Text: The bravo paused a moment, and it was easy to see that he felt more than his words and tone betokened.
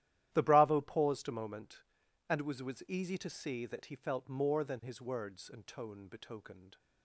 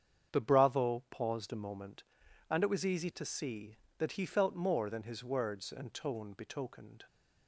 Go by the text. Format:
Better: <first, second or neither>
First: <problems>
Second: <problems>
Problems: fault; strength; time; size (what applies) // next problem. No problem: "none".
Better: second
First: starts louder than the rest; strong; until 1.3 s; 13 dB // says "was" twice; at 2.6 s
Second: starts louder than the rest; strong; until 1.4 s; 8 dB